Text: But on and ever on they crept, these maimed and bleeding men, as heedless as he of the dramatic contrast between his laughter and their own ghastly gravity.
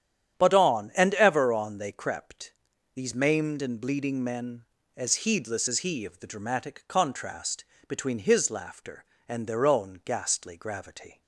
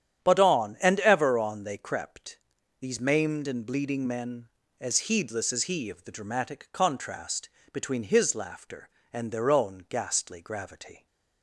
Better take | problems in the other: neither | starts louder than the rest; strong; the same in both // pauses between "contrast" and "between"; slight; the same in both

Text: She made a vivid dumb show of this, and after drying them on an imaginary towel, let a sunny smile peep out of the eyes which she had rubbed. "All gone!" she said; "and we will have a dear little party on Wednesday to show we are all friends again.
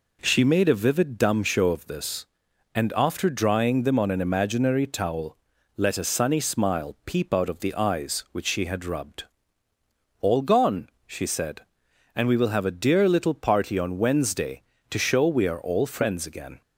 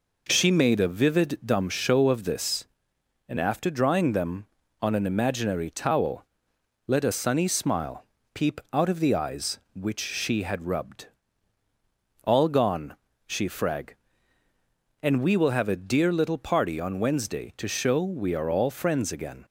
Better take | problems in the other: first | pauses between "smile" and "peep"; slight; at 8.0 s; 0.30 s long // says "frag" for "said"; at 13.4 s

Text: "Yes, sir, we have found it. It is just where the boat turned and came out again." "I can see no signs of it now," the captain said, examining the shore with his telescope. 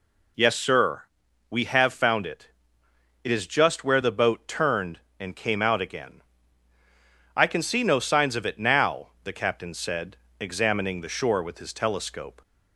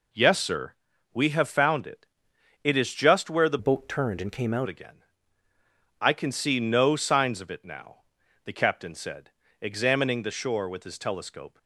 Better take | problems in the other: first | changes voice from "boat" to "out"; from 3.5 to 4.6 s; 1.1 s long

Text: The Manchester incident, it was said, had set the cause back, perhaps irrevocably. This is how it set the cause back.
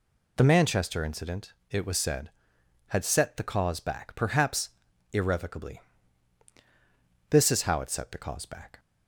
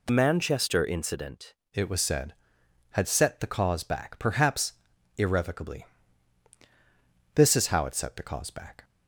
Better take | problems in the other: first | changes voice from "Manchester" to "incident"; from 0.0 to 1.5 s; 1.5 s long // pauses between "perhaps" and "irrevocably"; at 4.7 s; 0.44 s long; also in the first

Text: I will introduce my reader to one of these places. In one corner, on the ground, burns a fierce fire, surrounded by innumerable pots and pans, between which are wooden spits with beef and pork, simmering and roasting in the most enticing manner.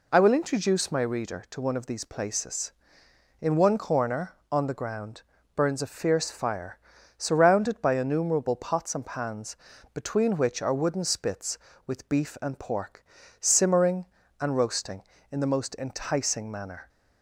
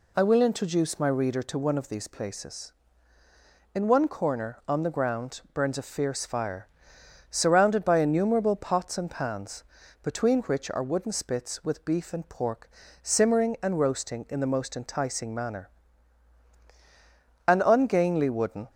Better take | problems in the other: first | goes on to say "An ungainly wooden"; noticeable; from 17.4 s on; 1.2 s long

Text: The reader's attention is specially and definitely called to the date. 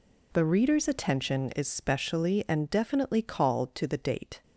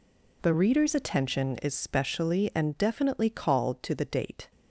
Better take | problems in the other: neither | none

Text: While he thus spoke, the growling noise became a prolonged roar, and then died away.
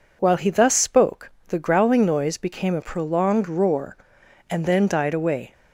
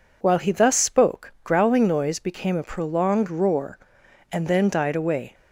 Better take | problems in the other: first | skips "the"; at 1.3 s

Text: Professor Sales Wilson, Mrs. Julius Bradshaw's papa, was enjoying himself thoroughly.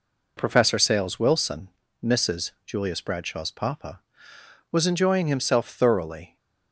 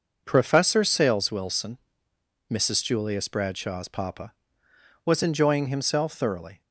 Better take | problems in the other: neither | none

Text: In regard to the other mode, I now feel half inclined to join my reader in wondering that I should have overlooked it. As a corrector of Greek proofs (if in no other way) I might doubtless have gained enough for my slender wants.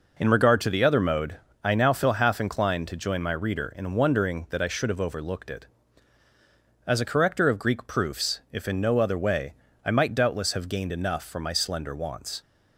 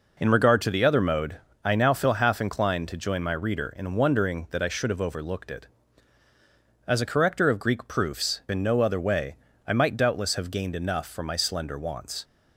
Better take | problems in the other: first | skips "if"; at 8.4 s

